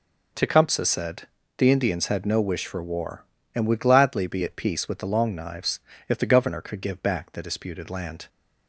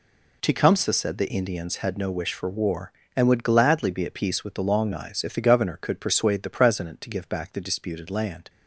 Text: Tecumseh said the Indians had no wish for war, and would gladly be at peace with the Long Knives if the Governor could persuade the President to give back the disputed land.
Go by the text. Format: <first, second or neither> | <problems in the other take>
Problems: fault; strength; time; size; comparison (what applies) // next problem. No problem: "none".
second | pauses between "said" and "the"; slight; at 1.2 s; 0.30 s long // pauses between "Knives" and "if"; slight; at 5.7 s; 0.30 s long // skips "persuade the President to"; at 6.8 s